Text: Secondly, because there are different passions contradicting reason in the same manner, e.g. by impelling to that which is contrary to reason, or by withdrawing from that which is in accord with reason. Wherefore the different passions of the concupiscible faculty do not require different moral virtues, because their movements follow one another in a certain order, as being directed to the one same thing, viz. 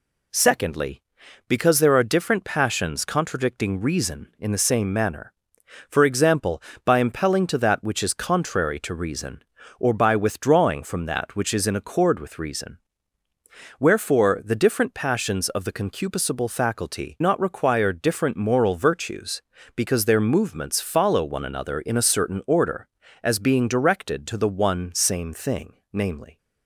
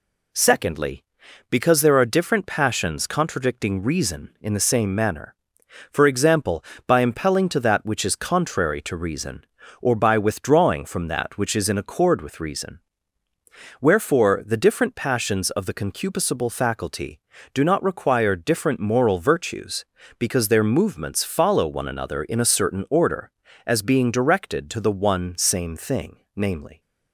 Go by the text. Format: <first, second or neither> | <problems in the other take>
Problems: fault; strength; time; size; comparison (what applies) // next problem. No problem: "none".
second | skips "do"; at 17.1 s